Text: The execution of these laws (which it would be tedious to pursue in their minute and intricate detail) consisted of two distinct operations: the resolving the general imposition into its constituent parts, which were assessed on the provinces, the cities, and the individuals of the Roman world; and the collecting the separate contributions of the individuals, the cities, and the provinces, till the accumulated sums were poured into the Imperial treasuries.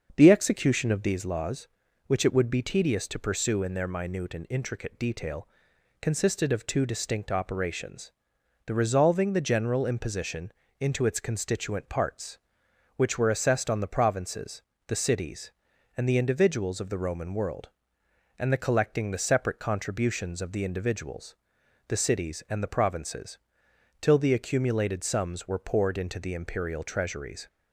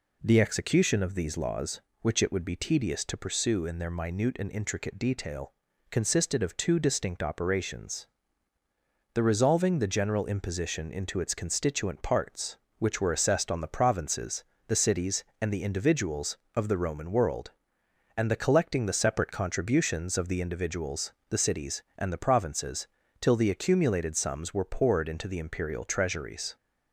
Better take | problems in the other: second | starts louder than the rest; until 1.3 s; 6.5 dB // pauses between "imposition" and "into"; slight; at 10.5 s; 0.30 s long

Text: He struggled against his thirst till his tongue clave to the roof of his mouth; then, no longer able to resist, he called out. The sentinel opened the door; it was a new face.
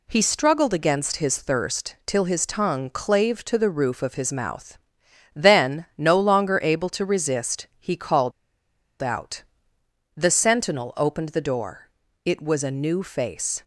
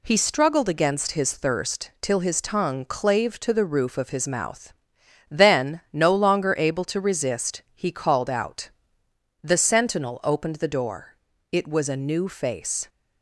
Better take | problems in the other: second | pauses between "called" and "out"; noticeable; at 8.3 s; 0.69 s long

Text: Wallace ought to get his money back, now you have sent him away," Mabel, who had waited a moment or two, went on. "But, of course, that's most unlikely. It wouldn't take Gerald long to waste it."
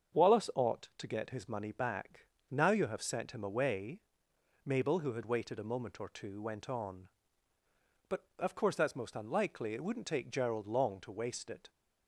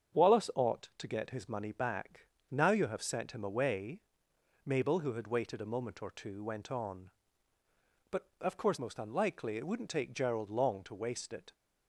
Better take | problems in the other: first | starts louder than the rest; strong; until 1.2 s; 7.5 dB; strong in the first // skips "that's"; at 8.7 s

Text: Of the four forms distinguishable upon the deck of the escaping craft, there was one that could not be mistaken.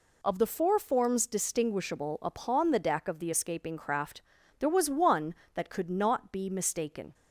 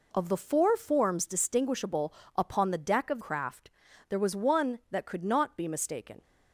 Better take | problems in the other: first | pauses between "distinguishable" and "upon"; slight; at 2.1 s; 0.22 s long // skips "the escaping"; at 3.2 s

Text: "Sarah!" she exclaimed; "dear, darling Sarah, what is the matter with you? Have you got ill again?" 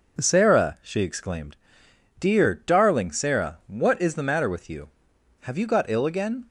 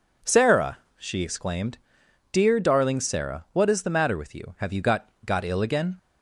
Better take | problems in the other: first | says "got" twice; at 5.2 s

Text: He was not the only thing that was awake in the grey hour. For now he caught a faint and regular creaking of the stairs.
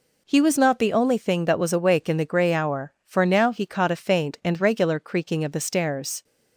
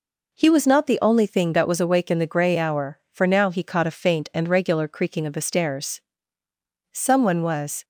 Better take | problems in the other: first | goes on to say "Someone was"; noticeable; from 6.9 s on; 0.92 s long

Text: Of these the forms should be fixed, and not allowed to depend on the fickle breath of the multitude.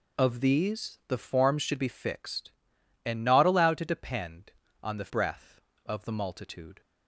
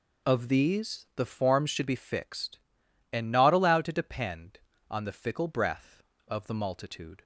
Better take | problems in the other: second | skips "fickle"; at 5.0 s

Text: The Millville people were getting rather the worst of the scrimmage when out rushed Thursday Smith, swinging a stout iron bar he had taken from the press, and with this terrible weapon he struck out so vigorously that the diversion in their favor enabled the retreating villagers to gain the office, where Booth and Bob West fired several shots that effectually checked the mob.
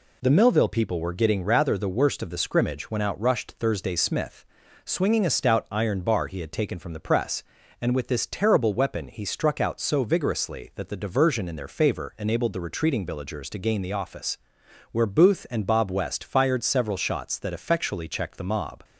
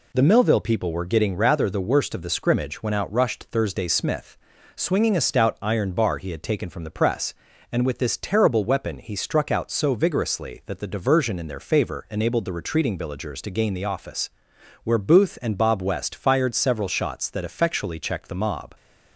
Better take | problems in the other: neither | none

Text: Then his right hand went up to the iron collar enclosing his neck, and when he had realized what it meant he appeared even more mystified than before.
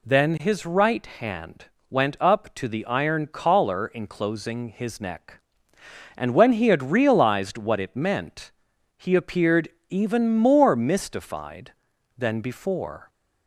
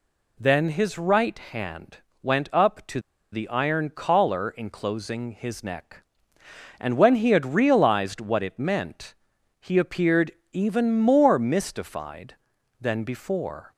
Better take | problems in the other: first | pauses between "hand" and "went"; slight; at 1.9 s; 0.24 s long; slight in the first // pauses between "to" and "the"; slight; at 2.9 s; 0.33 s long // pauses between "meant" and "he"; noticeable; at 9.1 s; 0.46 s long; noticeable in the first // pauses between "appeared" and "even"; slight; at 10.3 s; 0.20 s long; slight in the first

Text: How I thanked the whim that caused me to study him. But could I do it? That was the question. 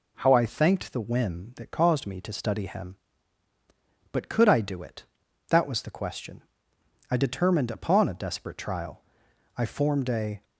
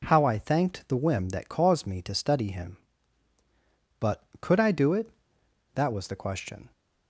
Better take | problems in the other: second | goes on to say "I determined upon a desperate trial I formed a"; strong; from 7.0 s on; 3.3 s long

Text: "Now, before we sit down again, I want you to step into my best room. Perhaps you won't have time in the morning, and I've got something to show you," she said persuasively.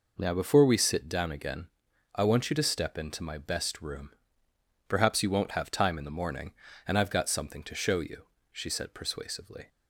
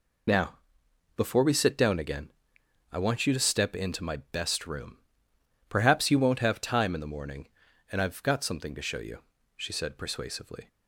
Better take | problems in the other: first | loses the start of "Now"; at 0.2 s; 50 ms

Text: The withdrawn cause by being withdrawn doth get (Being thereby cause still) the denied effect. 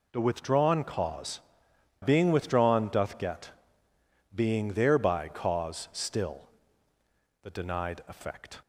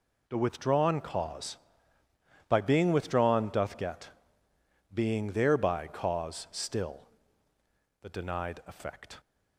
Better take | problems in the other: second | skips "by"; at 1.7 s

